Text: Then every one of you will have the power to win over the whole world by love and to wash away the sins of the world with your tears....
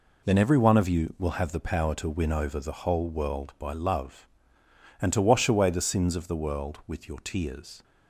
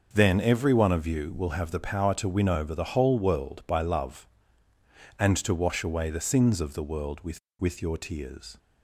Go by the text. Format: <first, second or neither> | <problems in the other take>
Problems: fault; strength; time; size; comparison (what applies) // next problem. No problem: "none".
first | starts louder than the rest; noticeable; until 1.1 s; 6 dB // says "with" twice; at 7.5 s